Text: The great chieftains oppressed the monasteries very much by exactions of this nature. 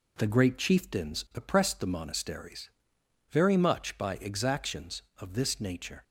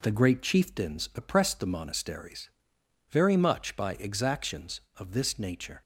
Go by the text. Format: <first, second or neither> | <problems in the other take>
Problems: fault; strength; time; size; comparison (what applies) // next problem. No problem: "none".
neither | pauses between "monasteries" and "very"; noticeable; the same in both